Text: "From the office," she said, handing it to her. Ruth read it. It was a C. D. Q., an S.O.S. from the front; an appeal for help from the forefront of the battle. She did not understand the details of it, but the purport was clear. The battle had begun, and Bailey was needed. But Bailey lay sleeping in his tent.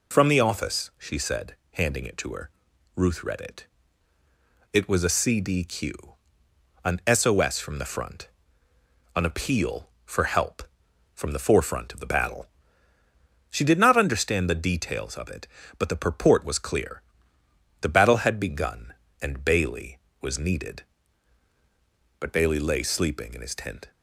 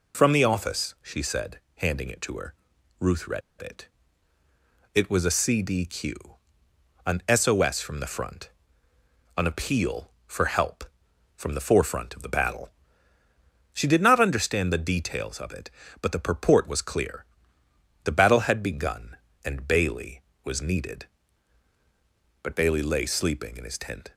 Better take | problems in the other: first | pauses between "read" and "it"; slight; at 3.4 s; 0.20 s long

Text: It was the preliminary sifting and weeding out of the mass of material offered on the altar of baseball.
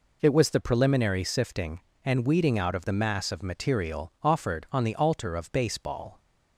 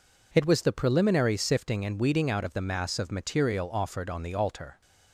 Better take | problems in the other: first | stops before "of baseball"; at 4.8 s

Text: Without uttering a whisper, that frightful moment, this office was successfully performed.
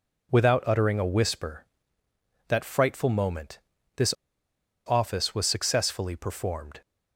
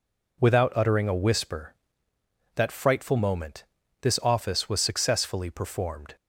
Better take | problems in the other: second | pauses between "this" and "office"; noticeable; at 4.1 s; 0.72 s long

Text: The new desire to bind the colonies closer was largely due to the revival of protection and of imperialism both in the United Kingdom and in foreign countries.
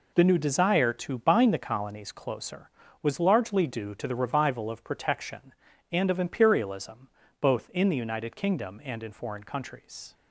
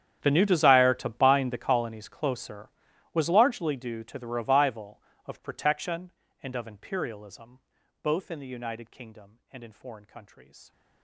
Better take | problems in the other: first | gets quieter; strong; throughout; 22 dB // pauses between "imperialism" and "both"; at 7.5 s; 0.44 s long; slight in the first

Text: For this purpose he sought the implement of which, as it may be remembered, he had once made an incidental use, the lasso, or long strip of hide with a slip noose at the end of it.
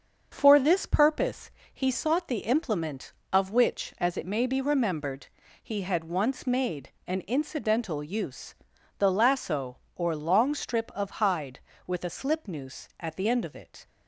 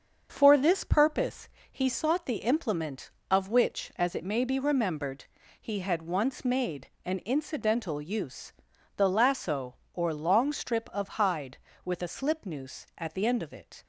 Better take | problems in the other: neither | starts louder than the rest; the same in both // pauses between "purpose" and "he"; slight; the same in both // pauses between "made" and "an"; slight; the same in both

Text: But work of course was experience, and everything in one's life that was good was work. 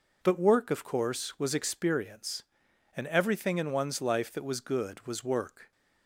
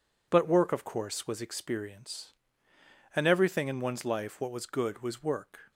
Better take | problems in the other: first | says "what" for "that"; at 4.3 s

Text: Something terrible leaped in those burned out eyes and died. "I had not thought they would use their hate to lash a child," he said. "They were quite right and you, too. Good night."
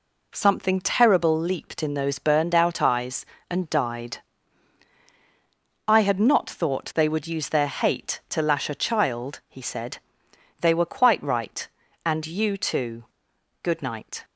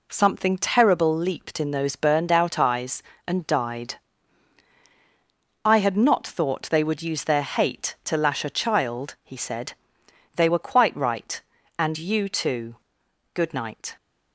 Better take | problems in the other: neither | none

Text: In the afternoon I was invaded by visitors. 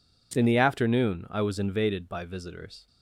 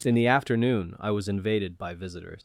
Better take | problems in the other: first | leaves "visitors" unfinished; at 2.3 s; 140 ms

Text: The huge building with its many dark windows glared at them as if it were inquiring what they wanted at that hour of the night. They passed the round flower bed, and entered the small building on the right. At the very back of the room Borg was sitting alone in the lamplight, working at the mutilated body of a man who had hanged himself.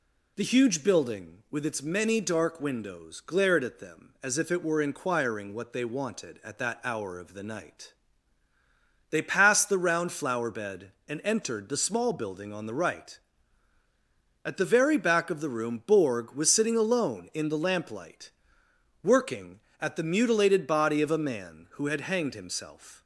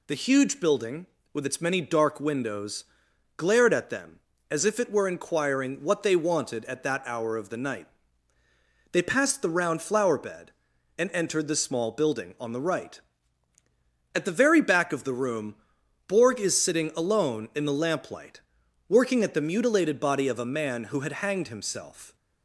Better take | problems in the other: first | pauses between "windows" and "glared"; noticeable; at 2.8 s; 0.54 s long // pauses between "room" and "Borg"; noticeable; at 15.5 s; 0.52 s long // says "is" for "was"; at 16.3 s

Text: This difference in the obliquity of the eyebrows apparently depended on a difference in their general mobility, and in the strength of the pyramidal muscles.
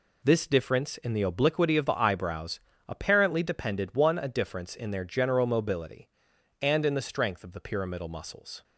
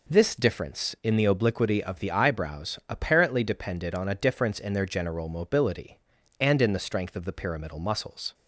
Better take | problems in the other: second | pauses between "eyebrows" and "apparently"; slight; at 2.5 s; 0.28 s long // says "one" for "on"; at 3.9 s

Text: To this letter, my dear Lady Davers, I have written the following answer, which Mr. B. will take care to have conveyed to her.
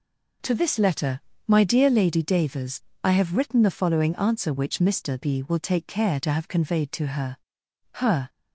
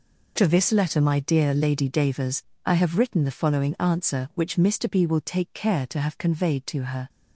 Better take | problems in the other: second | says "her" twice; at 7.9 s

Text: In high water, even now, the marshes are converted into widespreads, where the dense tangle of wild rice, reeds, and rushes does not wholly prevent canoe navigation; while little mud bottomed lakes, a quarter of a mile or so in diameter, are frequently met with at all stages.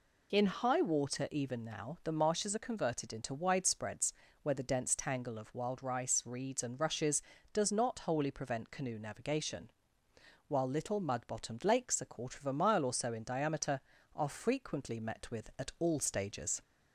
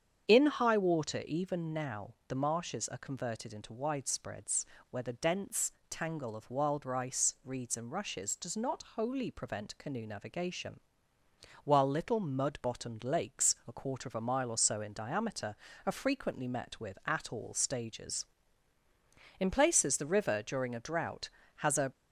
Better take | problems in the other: first | starts louder than the rest; strong; until 1.3 s; 8 dB // pauses between "dense" and "tangle"; slight; at 5.7 s; 0.18 s long // goes on to say "In places the river during a drought has a"; strong; from 19.3 s on; 2.5 s long

